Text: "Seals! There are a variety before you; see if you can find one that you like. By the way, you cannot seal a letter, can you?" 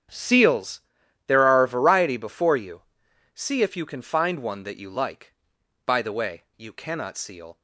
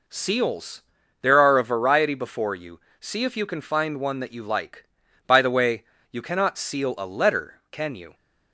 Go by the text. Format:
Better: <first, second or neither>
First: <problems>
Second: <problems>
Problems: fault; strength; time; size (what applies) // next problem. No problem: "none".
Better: second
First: starts louder than the rest; strong; until 1.6 s; 9 dB // stops before "a letter can you"; at 7.5 s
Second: none